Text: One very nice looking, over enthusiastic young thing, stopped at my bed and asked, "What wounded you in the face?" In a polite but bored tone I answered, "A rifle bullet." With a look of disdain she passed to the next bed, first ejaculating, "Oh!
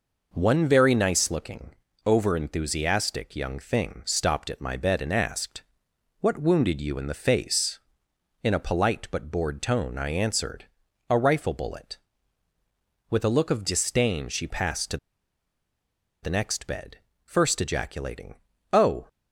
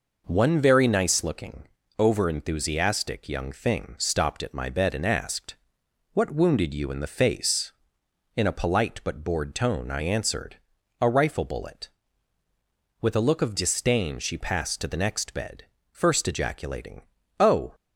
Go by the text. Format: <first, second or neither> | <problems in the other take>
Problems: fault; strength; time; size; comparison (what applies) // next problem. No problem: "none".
second | pauses between "to" and "the"; strong; at 14.9 s; 1.2 s long